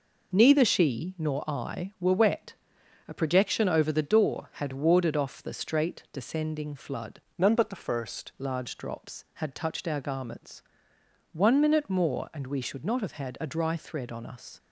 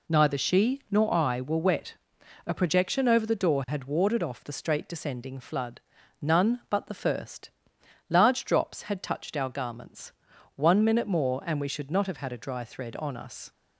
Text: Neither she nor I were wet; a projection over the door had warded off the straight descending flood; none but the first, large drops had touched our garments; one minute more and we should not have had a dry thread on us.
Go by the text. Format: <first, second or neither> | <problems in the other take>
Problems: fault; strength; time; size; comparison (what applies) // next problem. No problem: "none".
second | changes voice from "none" to "first"; from 7.3 to 8.3 s; 1.0 s long